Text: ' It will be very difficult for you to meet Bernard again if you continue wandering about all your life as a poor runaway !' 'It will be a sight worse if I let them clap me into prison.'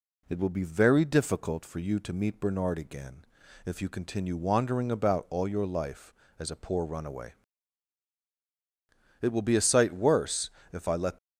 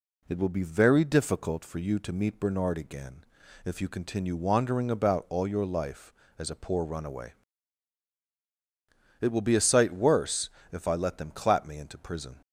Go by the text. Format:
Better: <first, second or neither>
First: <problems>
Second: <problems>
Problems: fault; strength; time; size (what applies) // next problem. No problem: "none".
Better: second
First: pauses between "again" and "if"; at 3.2 s; 0.40 s long // pauses between "worse" and "if"; slight; at 10.4 s; 0.22 s long // stops before "them clap me into prison"; at 11.1 s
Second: pauses between "again" and "if"; at 3.2 s; 0.40 s long // pauses between "worse" and "if"; slight; at 10.4 s; 0.22 s long